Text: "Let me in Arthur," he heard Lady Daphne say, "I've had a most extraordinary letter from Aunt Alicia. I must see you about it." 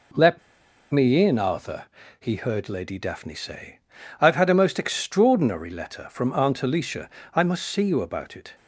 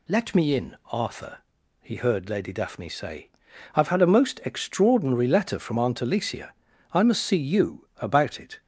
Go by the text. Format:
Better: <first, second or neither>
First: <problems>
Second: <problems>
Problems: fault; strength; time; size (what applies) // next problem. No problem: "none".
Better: second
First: pauses between "Let" and "me"; noticeable; at 0.3 s; 0.53 s long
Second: none